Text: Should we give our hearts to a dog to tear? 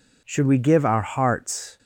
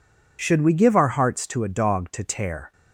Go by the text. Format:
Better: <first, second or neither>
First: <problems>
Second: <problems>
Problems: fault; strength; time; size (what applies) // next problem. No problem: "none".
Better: second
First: stops before "to a dog to tear"; at 1.7 s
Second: none